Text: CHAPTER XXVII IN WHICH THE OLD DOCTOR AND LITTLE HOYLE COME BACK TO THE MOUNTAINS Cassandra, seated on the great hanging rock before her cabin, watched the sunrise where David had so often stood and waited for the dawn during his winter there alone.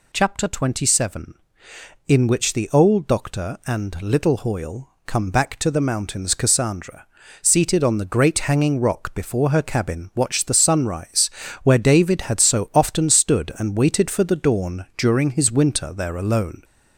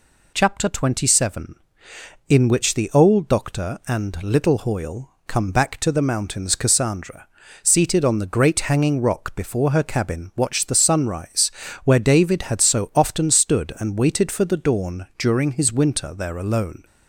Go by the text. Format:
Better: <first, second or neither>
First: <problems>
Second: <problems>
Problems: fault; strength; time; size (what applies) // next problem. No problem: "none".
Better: second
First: gets louder; slight; throughout; 2.5 dB // pauses between "HOYLE" and "COME"; slight; at 4.8 s; 0.16 s long // pauses between "sunrise" and "where"; slight; at 11.2 s; 0.32 s long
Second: pauses between "HOYLE" and "COME"; slight; at 5.1 s; 0.16 s long // pauses between "sunrise" and "where"; slight; at 11.5 s; 0.32 s long